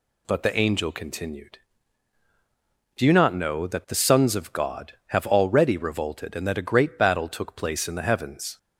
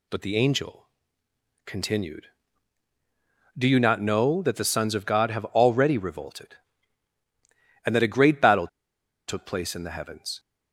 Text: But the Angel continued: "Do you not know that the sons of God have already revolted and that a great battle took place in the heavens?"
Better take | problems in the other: first | pauses between "Angel" and "continued"; noticeable; at 0.8 s; 0.78 s long // pauses between "battle" and "took"; noticeable; at 8.6 s; 0.60 s long

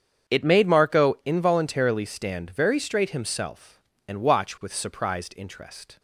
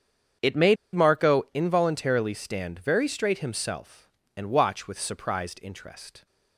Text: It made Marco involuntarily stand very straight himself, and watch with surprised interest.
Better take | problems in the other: first | starts louder than the rest; strong; until 1.7 s; 8 dB; strong in the first // pauses between "made" and "Marco"; slight; at 0.7 s; 0.19 s long

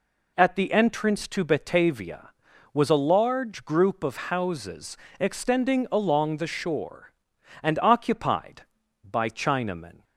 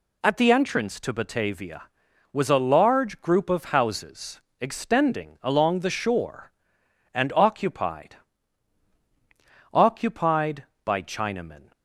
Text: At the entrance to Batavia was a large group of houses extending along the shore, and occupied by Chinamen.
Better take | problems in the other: first | pauses between "houses" and "extending"; slight; at 4.3 s; 0.20 s long; slight in the first // says "occupied" twice; at 9.7 s

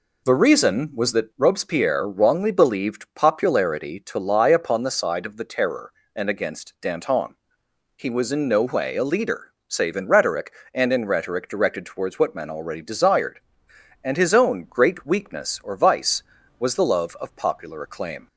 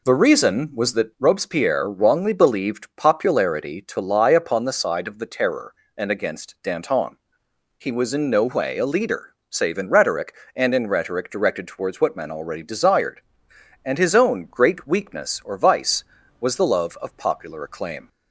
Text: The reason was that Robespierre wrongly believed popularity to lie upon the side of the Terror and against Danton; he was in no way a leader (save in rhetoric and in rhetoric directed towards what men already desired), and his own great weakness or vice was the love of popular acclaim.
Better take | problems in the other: neither | none

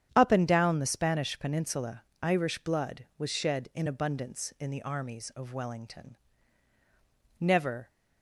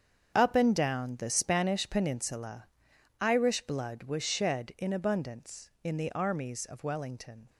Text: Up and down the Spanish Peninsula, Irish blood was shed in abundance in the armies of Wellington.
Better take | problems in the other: second | starts louder than the rest; strong; until 1.1 s; 9 dB; strong in the second // goes on to say "Never"; from 7.3 s on; 0.50 s long

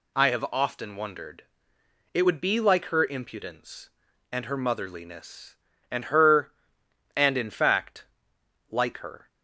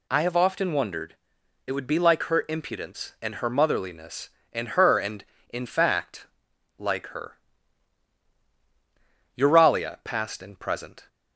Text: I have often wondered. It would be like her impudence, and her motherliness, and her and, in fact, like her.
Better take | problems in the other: first | goes on to say "Euralia Past and Present"; strong; from 9.3 s on; 1.7 s long

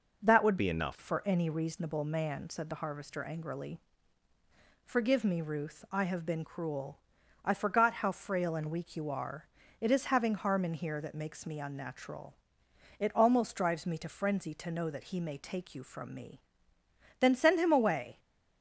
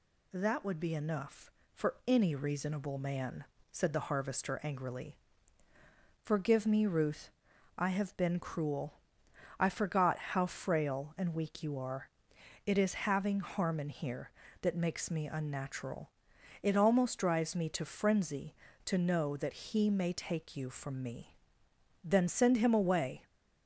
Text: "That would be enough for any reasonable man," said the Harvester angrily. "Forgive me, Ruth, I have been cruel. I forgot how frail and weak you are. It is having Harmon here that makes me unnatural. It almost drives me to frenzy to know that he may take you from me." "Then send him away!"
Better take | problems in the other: second | changes voice from "be" to "enough"; from 0.5 to 0.9 s; 0.4 s long

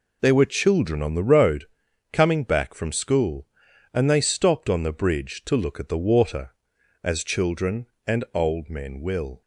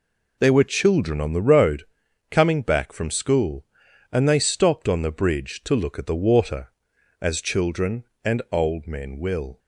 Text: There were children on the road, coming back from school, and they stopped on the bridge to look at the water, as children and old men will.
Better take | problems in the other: neither | none

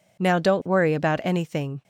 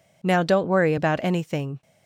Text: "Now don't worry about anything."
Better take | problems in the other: neither | none

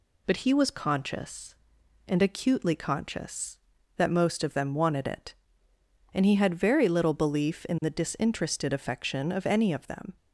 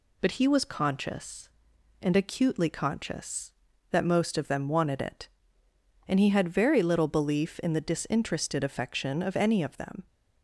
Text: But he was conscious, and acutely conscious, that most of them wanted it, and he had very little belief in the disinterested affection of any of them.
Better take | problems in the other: neither | none

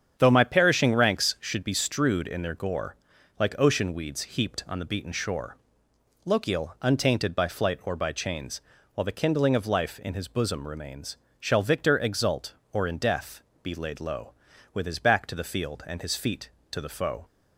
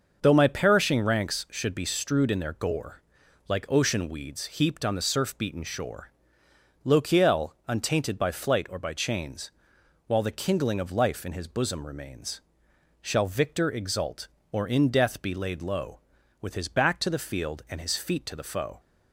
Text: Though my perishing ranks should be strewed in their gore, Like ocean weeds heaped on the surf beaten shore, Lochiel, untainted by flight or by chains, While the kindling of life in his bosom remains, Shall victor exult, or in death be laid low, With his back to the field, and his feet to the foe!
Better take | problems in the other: second | starts louder than the rest; strong; until 1.1 s; 8 dB // skips "surf"; at 4.8 s // pauses between "death" and "be"; slight; at 13.4 s; 0.22 s long

